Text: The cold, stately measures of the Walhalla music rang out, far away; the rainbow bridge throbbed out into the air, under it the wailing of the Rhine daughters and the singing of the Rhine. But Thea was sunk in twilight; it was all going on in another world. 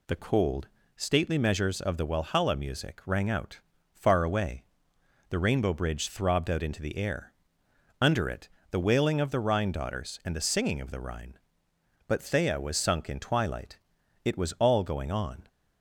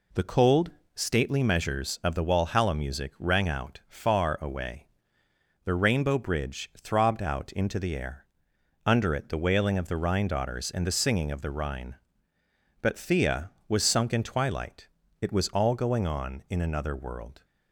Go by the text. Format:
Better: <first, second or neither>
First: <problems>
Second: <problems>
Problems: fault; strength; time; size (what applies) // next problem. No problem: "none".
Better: second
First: pauses between "it" and "the"; slight; at 8.4 s; 0.22 s long // stops before "in another world"; at 15.4 s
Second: none